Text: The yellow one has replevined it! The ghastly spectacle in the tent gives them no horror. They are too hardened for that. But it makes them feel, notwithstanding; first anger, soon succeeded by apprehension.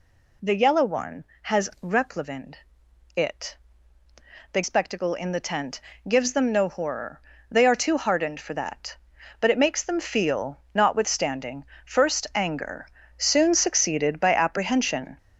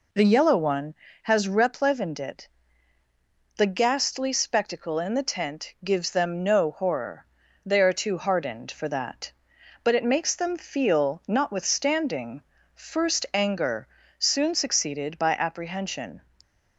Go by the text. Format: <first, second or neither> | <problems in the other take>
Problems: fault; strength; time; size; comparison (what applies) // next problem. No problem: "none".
second | pauses between "replevined" and "it"; noticeable; at 2.5 s; 0.58 s long // skips "ghastly"; at 4.6 s // pauses between "tent" and "gives"; slight; at 5.8 s; 0.26 s long